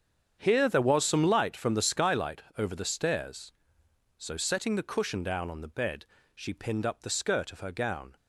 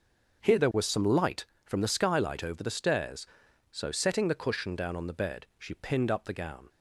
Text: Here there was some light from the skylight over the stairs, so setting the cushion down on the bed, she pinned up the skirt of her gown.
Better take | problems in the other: first | starts louder than the rest; until 1.6 s; 6.5 dB; strong in the first // skips "skirt of her"; at 6.3 s

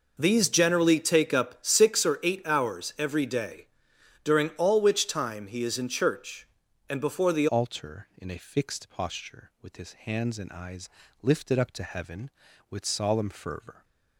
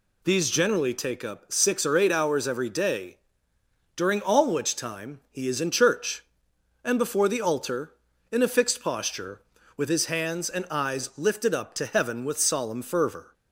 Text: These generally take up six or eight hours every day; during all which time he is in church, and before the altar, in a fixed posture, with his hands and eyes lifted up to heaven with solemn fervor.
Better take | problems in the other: second | changes voice at "altar"; from 7.4 s on; 6.4 s long // pauses between "eyes" and "lifted"; slight; at 10.8 s; 0.34 s long

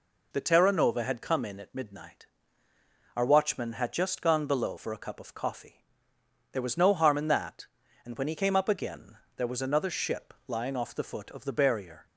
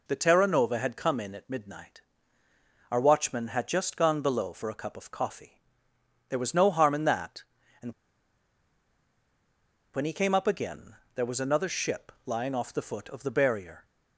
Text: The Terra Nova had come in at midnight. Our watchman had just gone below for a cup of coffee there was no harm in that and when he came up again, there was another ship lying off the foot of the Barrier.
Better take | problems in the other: first | pauses between "coffee" and "there"; noticeable; at 5.5 s; 0.70 s long; noticeable in the first // pauses between "and" and "when"; strong; at 7.9 s; 2.0 s long

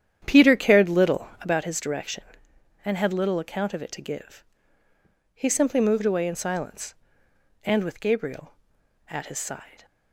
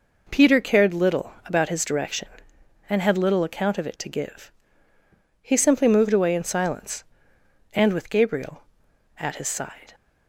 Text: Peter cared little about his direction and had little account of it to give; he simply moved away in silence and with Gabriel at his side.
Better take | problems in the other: second | starts louder than the rest; strong; until 1.5 s; 9.5 dB

